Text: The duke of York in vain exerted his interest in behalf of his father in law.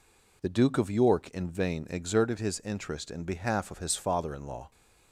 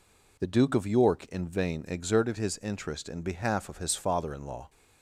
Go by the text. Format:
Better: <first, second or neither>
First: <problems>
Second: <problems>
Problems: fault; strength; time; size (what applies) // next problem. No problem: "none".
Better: neither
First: none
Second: none